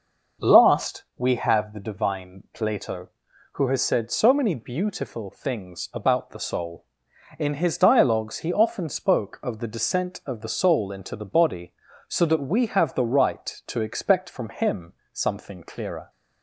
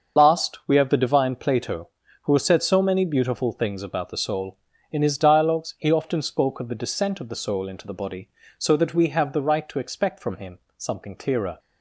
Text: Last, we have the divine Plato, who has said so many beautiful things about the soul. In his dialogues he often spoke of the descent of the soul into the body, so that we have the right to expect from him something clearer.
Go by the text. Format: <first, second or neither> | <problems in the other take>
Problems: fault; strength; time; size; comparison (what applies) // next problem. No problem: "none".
first | loses the start of "Last"; at 0.1 s; 45 ms // starts louder than the rest; until 1.2 s; 6.5 dB // pauses between "him" and "something"; slight; at 10.5 s; 0.18 s long; slight in the first